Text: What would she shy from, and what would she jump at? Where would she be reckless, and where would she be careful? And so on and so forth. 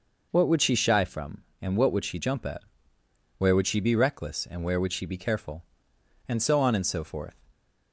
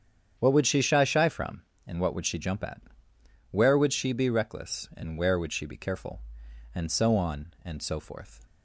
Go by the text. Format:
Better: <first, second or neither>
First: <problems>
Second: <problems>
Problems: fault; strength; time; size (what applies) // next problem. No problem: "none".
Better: first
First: none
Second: starts louder than the rest; strong; until 1.4 s; 8.5 dB // says "shy" twice; at 1.0 s